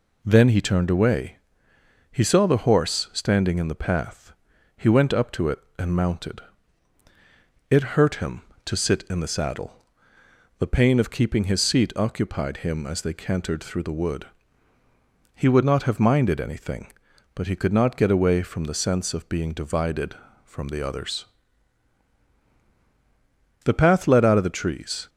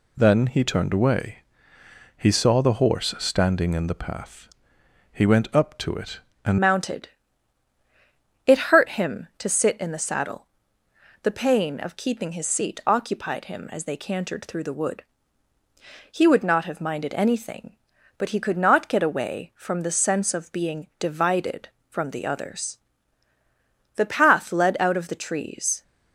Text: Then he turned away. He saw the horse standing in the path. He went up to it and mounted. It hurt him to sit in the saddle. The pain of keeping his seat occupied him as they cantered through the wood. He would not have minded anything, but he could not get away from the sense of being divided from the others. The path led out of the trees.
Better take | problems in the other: first | changes voice at "mounted"; from 6.6 s on; 19.2 s long

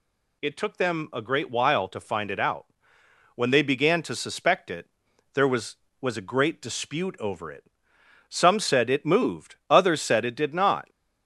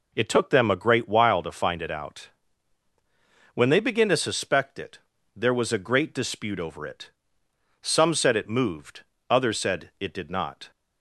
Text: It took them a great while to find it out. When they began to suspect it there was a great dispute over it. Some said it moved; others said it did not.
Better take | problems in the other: second | pauses between "it" and "there"; noticeable; at 4.8 s; 0.48 s long; also in the second // says "was" twice; at 6.0 s

